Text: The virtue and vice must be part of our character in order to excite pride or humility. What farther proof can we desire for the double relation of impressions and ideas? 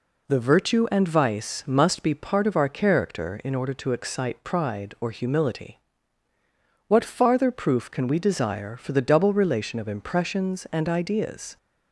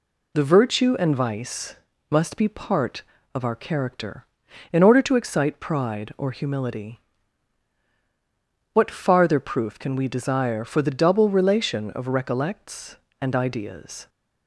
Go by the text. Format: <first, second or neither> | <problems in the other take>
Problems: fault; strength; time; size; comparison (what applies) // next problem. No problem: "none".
first | pauses between "vice" and "must"; slight; at 1.7 s; 0.34 s long // says "recollects" for "impressions"; at 12.0 s